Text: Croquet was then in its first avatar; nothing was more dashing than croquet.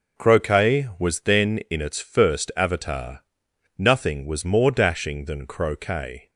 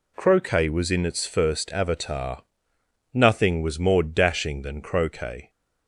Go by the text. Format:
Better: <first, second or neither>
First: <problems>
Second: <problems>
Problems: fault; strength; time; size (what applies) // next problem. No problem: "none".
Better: first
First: none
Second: skips "then"; at 0.9 s